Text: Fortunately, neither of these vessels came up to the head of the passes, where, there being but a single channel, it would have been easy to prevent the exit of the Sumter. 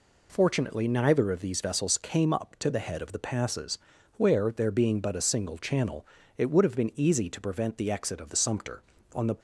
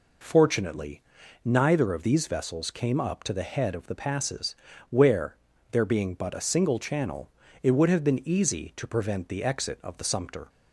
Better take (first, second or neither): second